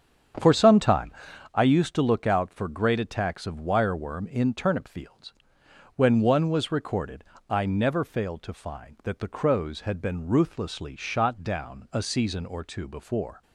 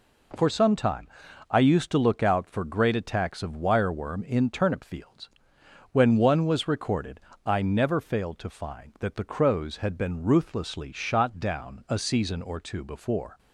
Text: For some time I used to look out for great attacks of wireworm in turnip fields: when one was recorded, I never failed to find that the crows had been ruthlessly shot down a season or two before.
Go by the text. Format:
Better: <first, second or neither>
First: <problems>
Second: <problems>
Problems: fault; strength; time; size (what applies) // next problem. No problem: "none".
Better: second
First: starts louder than the rest; strong; until 1.5 s; 8 dB // pauses between "time" and "I"; at 1.1 s; 0.42 s long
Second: pauses between "time" and "I"; at 1.0 s; 0.42 s long